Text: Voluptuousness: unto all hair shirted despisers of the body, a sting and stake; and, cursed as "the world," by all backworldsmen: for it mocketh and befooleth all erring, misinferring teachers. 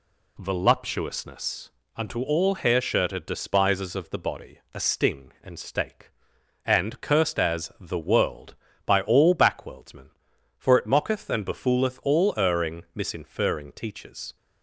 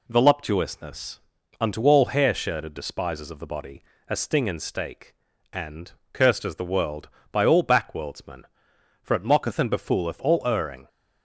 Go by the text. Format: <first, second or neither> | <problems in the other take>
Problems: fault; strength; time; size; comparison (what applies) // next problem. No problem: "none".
first | stops before "misinferring teachers"; at 10.8 s